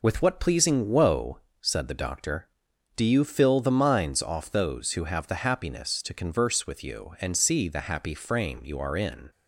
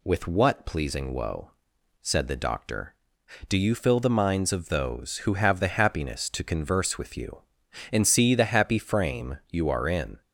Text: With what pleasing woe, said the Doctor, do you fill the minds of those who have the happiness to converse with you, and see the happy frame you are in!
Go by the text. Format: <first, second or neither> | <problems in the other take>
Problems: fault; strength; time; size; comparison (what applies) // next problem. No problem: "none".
second | says "off" for "of"; at 4.2 s